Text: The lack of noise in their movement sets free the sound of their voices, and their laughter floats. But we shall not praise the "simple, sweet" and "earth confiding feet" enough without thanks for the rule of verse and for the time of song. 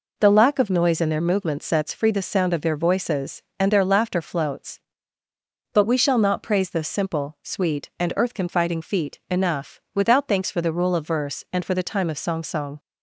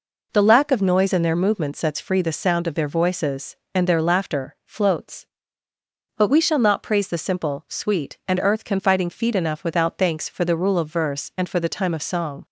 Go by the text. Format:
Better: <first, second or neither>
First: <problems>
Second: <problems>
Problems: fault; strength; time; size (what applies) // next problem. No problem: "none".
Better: second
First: says "song" twice; at 12.4 s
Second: none